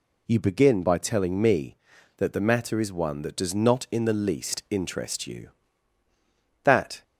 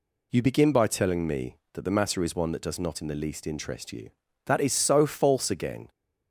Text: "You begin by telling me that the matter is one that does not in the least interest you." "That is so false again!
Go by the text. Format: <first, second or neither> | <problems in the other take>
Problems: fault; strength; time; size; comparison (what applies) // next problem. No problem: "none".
second | stops before "is so false again"; at 7.0 s